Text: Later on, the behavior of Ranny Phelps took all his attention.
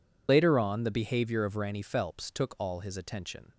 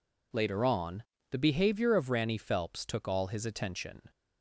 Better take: second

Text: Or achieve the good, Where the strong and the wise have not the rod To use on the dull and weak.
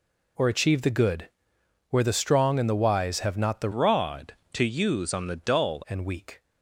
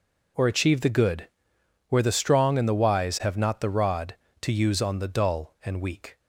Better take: second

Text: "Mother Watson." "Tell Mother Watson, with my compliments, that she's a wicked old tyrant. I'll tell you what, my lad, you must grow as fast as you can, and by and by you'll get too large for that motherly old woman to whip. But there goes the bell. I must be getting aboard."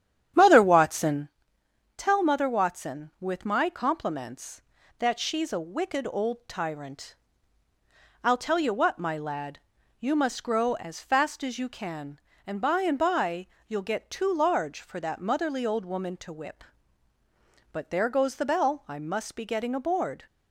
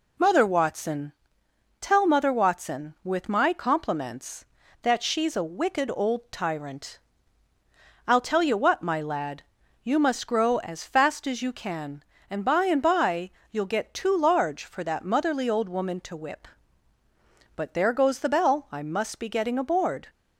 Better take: second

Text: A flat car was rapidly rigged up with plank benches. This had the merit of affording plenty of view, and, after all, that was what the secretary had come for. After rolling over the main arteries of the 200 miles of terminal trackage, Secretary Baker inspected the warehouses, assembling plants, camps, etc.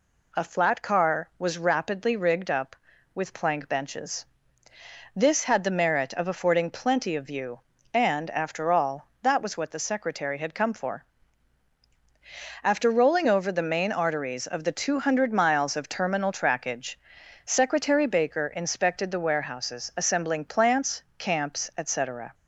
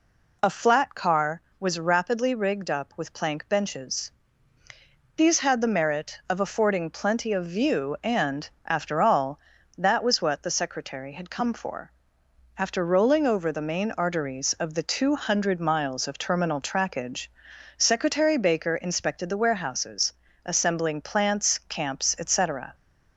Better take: first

